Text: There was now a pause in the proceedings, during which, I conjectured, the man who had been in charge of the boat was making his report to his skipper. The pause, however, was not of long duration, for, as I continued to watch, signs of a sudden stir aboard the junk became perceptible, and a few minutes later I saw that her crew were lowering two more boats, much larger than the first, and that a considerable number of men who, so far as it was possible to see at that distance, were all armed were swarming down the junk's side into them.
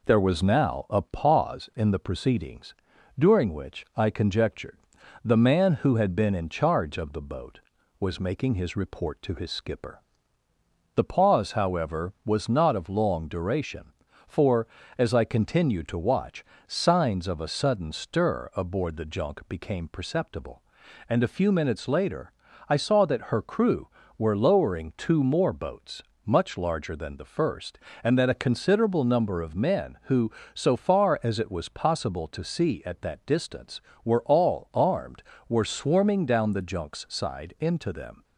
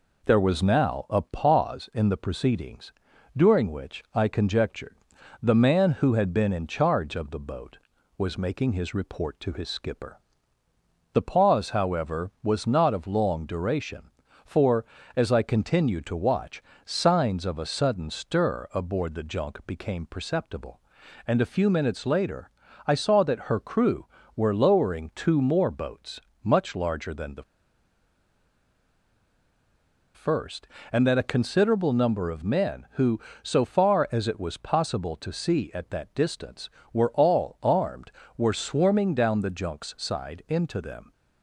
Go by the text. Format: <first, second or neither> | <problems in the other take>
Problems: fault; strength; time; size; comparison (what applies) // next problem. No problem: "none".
first | pauses between "later" and "I"; at 22.4 s; 0.38 s long; also in the first // pauses between "the" and "first"; strong; at 27.4 s; 2.7 s long